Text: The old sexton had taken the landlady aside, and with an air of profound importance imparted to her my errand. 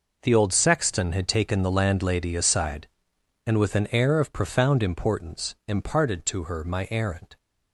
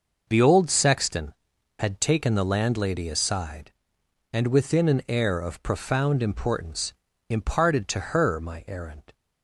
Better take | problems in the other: first | says "within" for "with"; at 4.4 s // pauses between "importance" and "imparted"; slight; at 6.9 s; 0.36 s long

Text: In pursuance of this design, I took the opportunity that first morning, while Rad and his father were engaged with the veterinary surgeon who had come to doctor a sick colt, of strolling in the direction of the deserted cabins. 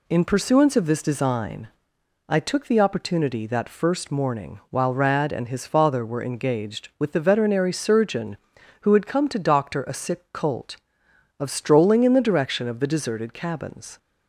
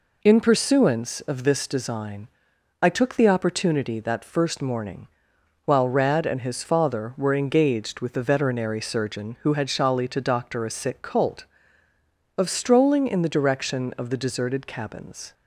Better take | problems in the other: first | says "shali" for "come"; at 9.6 s

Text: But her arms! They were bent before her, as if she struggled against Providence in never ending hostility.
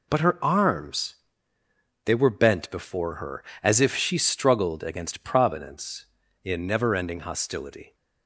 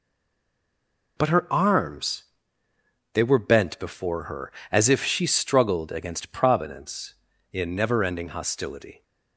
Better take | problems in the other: first | stays silent before the first word; noticeable; until 1.1 s; 1.1 s long

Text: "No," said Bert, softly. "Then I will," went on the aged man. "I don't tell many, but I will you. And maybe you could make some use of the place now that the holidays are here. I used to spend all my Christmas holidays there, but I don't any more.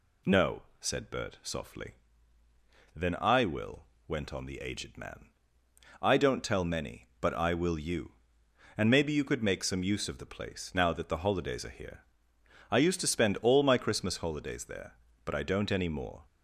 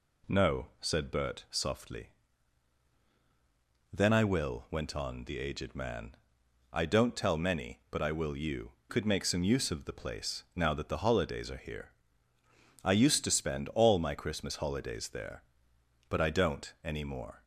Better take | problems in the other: first | skips "And maybe you"; at 8.8 s

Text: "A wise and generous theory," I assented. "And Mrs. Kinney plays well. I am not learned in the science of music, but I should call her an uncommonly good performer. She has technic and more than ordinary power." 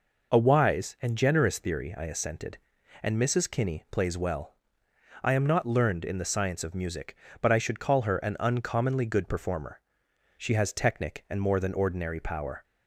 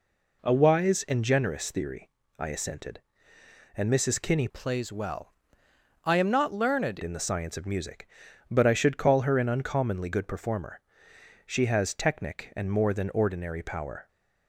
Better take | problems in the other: first | changes voice from "plays" to "learned"; from 4.4 to 6.9 s; 2.5 s long

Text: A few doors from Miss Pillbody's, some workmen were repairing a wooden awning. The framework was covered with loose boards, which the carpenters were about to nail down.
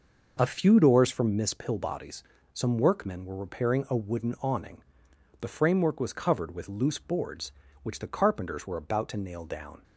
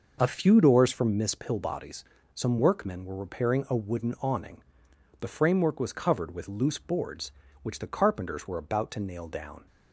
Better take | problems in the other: neither | none

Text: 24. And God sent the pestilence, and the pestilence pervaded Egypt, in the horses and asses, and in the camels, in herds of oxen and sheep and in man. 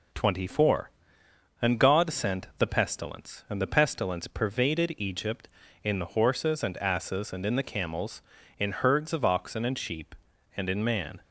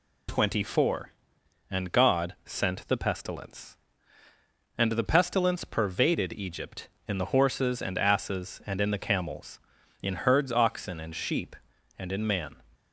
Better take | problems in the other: first | skips "of"; at 10.5 s

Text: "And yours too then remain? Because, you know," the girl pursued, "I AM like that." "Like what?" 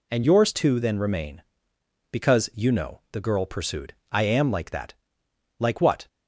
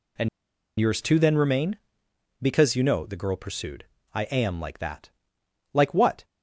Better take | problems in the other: first | pauses between "And" and "yours"; noticeable; at 0.2 s; 0.51 s long

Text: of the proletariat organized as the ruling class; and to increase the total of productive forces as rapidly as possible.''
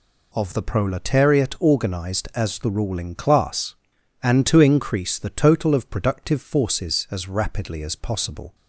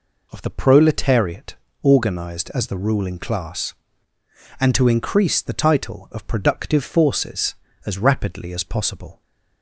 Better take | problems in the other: first | pauses between "proletariat" and "organized"; slight; at 1.5 s; 0.28 s long // says "title" for "total"; at 5.5 s

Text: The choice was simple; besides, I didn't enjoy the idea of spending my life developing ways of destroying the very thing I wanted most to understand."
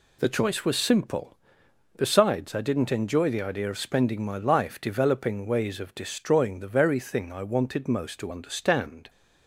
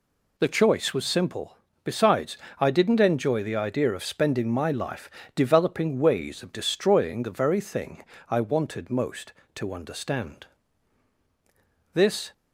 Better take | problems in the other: first | pauses between "life" and "developing"; slight; at 5.0 s; 0.28 s long // pauses between "thing" and "I"; slight; at 8.0 s; 0.28 s long // goes on to say "This"; slight; from 11.9 s on; 0.40 s long

